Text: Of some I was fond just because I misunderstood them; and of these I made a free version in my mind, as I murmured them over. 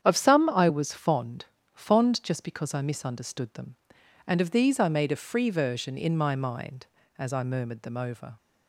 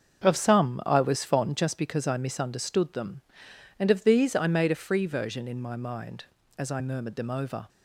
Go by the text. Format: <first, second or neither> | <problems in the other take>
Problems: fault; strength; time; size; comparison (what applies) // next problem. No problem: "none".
second | starts louder than the rest; strong; until 1.0 s; 8.5 dB; also in the second // says "fond" twice; at 1.7 s